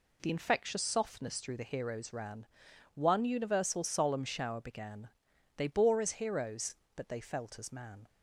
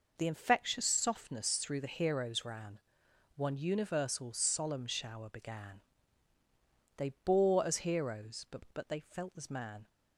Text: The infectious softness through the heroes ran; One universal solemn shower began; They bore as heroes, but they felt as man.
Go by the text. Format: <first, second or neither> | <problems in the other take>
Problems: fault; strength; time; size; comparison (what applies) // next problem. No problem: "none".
first | says "but" twice; at 8.7 s